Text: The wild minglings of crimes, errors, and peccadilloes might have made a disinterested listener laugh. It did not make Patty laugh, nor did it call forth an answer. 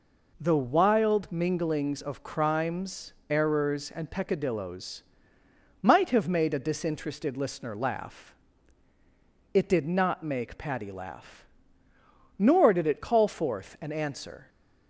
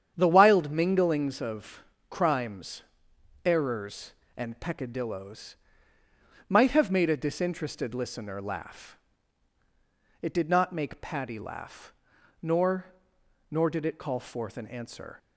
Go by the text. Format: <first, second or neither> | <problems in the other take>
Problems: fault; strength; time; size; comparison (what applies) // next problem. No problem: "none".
first | starts louder than the rest; strong; until 1.1 s; 8.5 dB // pauses between "of" and "crimes"; slight; at 1.8 s; 0.26 s long // pauses between "peccadilloes" and "might"; noticeable; at 5.5 s; 0.92 s long; noticeable in the first // says "nor" twice; at 13.4 s